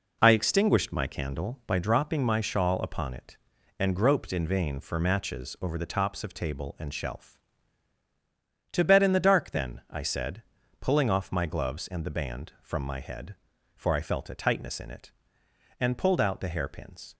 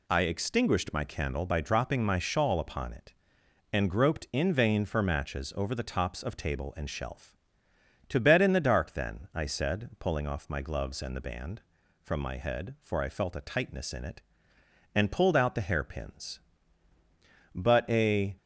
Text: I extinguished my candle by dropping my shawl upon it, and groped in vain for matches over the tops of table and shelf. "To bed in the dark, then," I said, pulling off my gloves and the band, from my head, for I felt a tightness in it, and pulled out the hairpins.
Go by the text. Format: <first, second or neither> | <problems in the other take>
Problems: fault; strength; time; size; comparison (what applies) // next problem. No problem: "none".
first | goes on to say "But a"; noticeable; from 17.5 s on; 0.82 s long